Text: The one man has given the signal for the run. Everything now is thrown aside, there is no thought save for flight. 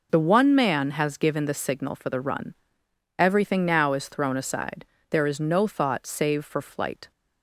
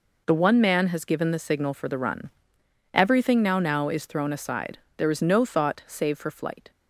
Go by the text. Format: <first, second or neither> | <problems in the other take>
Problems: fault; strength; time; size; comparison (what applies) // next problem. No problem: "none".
first | says "now" twice; at 3.5 s